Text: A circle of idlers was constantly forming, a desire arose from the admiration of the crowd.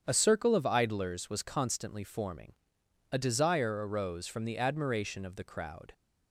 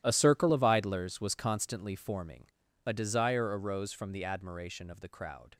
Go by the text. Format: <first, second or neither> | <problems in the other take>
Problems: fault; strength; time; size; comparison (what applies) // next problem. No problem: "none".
first | gets quieter; strong; throughout; 15.5 dB // starts louder than the rest; strong; until 1.0 s; 12.5 dB; strong in the first